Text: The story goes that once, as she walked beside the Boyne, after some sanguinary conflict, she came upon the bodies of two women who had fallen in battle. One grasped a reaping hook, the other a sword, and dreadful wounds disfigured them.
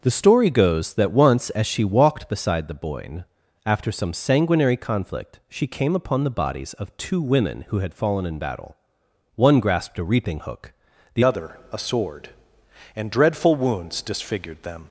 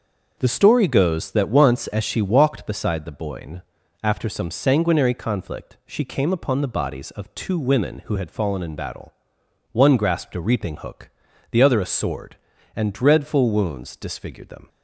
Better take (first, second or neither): second